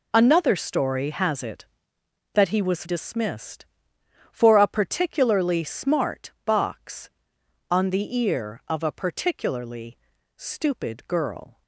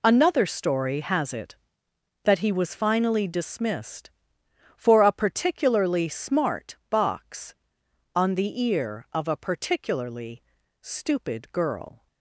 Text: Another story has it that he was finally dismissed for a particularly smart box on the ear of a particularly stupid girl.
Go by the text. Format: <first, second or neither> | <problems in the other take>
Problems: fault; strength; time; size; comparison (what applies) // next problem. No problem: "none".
second | skips "finally"; at 2.8 s // pauses between "particularly" and "stupid"; at 9.9 s; 0.40 s long; also in the second